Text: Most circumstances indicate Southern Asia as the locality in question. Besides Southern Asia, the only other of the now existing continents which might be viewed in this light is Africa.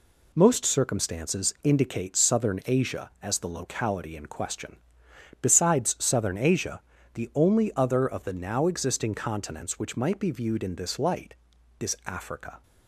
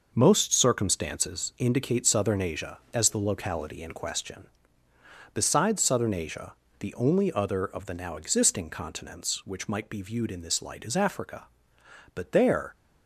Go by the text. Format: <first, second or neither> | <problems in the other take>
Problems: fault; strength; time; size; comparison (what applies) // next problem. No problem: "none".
first | goes on to say "But there"; noticeable; from 12.1 s on; 0.62 s long